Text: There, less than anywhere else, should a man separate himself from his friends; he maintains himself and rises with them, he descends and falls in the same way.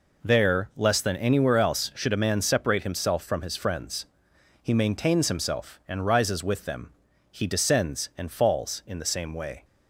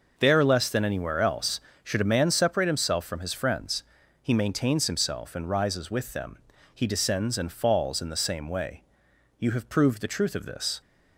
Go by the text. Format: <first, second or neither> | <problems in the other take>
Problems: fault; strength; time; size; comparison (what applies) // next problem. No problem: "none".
first | goes on to say "You have proved the truth of this"; from 9.3 s on; 1.4 s long